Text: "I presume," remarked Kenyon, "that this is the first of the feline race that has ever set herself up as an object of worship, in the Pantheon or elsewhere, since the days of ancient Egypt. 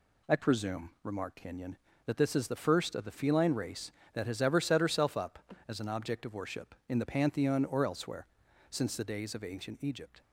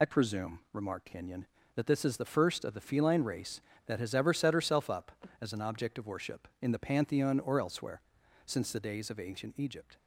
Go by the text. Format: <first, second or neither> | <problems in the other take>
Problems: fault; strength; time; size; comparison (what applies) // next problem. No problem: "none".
first | loses the start of "I"; at 0.0 s; 60 ms